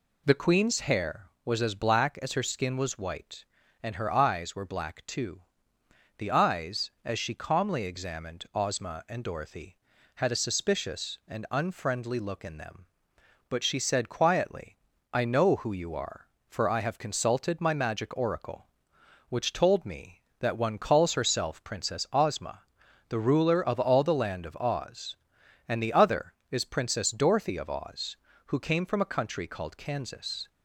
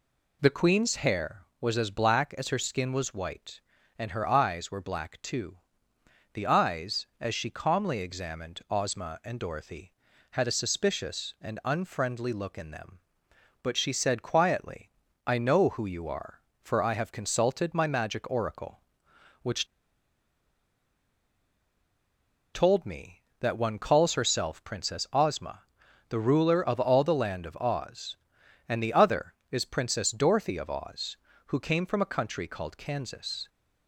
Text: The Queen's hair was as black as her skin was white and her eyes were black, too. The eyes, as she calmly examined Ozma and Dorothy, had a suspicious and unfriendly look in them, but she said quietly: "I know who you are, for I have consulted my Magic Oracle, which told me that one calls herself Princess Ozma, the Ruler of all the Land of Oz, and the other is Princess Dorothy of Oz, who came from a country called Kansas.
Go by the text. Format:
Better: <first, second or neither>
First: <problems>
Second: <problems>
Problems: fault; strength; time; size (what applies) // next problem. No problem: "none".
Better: first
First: none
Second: pauses between "which" and "told"; strong; at 19.6 s; 2.8 s long